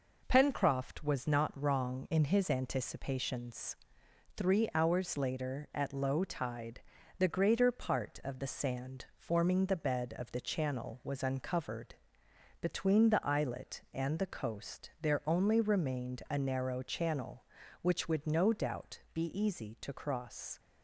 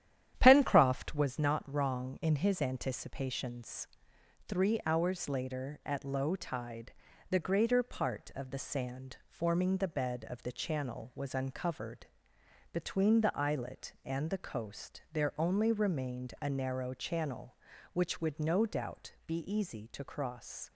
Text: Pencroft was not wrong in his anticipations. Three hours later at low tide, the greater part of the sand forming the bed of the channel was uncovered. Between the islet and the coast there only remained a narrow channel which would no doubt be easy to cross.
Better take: first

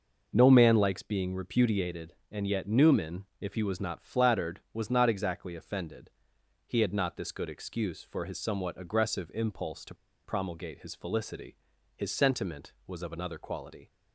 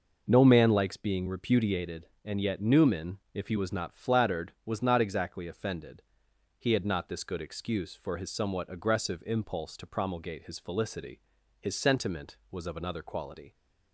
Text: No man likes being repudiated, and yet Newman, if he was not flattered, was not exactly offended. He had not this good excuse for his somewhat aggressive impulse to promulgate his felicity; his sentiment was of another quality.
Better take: second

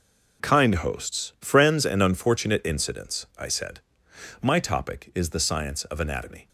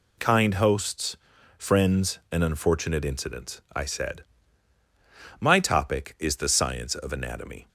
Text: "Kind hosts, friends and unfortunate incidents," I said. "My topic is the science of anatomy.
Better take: neither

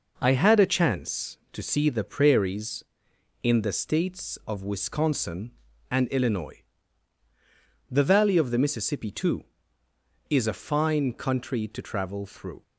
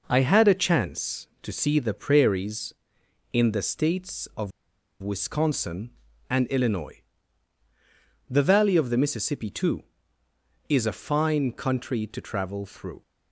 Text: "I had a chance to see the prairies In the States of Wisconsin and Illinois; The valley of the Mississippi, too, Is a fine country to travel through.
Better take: first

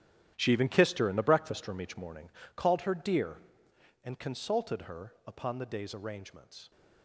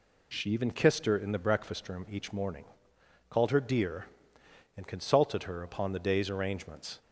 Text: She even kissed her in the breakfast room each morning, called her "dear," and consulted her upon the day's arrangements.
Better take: second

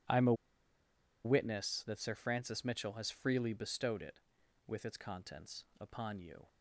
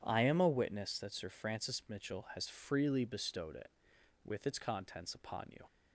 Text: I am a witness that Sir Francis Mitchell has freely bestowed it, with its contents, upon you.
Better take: second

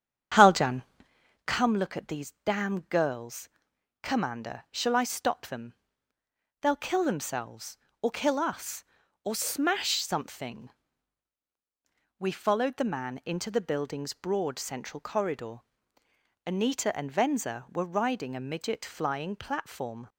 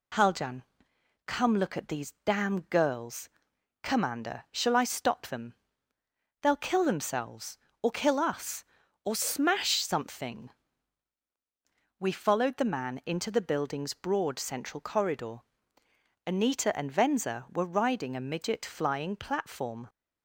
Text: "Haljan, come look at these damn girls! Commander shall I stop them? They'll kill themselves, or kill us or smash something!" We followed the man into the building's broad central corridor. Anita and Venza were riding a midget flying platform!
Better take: second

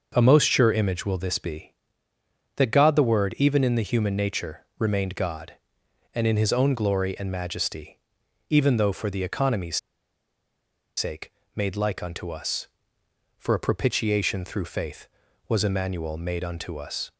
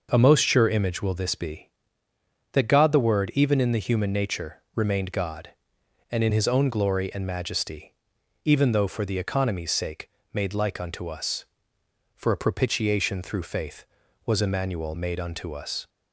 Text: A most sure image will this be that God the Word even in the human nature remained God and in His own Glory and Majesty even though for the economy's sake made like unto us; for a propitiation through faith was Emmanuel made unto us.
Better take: second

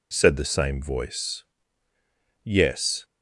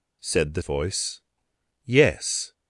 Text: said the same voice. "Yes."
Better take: first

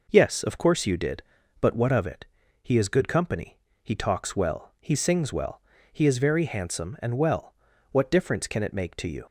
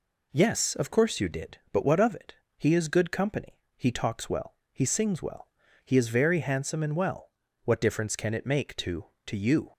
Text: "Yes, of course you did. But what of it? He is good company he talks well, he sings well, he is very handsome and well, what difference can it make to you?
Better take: first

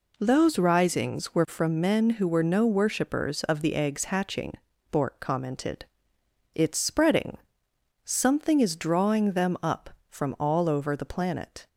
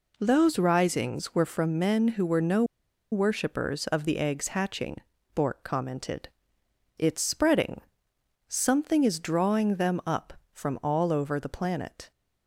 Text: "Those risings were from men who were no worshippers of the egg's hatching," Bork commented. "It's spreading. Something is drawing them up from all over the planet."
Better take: first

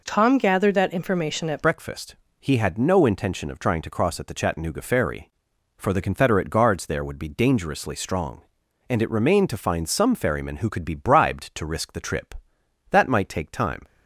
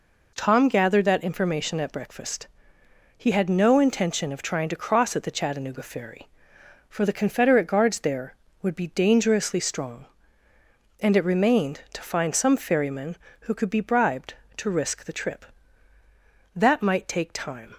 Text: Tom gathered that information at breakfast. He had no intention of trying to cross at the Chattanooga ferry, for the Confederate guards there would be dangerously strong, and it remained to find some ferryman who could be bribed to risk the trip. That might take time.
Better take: second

